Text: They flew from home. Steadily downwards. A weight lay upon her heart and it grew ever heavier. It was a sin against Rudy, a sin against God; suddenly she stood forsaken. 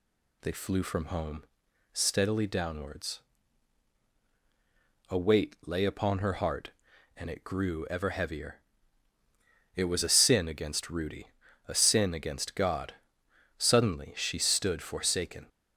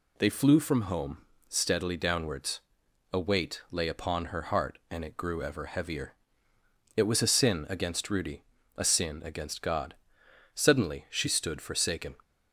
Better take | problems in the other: neither | none

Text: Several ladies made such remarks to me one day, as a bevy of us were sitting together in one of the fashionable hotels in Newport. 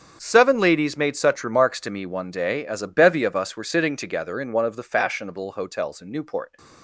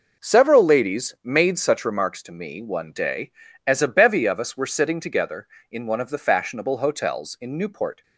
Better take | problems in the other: second | starts louder than the rest; strong; until 1.2 s; 7 dB // says "Seven" for "Several"; at 0.2 s

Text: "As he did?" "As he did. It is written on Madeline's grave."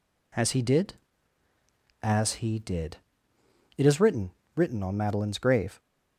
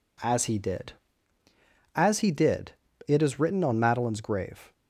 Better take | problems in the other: second | says "written" twice; at 4.5 s

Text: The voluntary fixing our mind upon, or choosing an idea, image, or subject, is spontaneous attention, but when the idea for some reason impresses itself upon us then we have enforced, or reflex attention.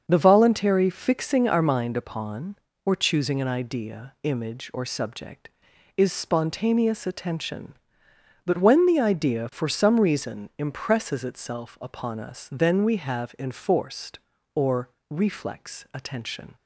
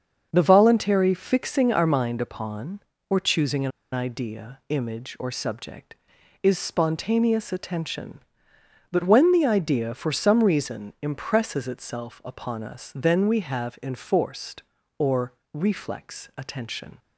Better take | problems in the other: first | starts louder than the rest; until 1.3 s; 7 dB; also in the first // pauses between "an" and "idea"; slight; at 3.7 s; 0.23 s long // pauses between "or" and "reflex"; slight; at 15.3 s; 0.22 s long; slight in the first

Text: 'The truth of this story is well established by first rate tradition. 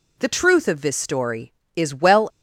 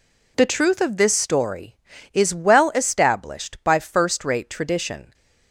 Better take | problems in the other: second | stops before "established by first rate tradition"; at 2.2 s

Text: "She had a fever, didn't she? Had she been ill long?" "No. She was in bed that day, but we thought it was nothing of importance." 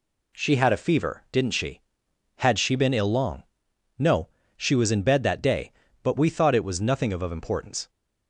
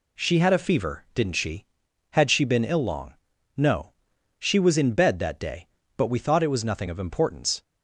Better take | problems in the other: second | says "of" twice; at 7.2 s

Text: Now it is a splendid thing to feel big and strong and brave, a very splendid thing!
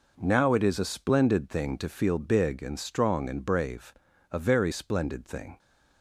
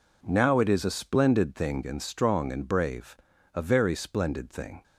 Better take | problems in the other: first | skips "to feel big"; at 1.8 s

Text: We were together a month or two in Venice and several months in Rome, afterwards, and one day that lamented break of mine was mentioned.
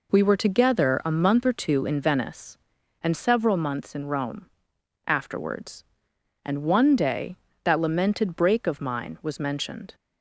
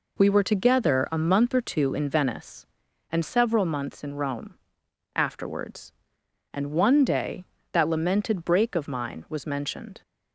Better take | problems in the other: neither | none

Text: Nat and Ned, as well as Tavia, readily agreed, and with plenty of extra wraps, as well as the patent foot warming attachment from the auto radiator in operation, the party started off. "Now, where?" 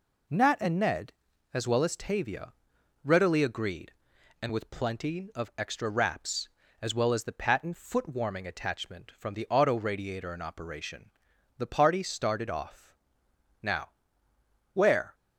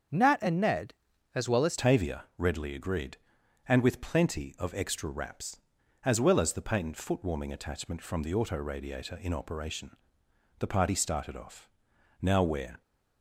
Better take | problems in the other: first | starts louder than the rest; until 1.5 s; 7 dB // changes voice at "Tavia"; from 1.7 s on; 11.1 s long

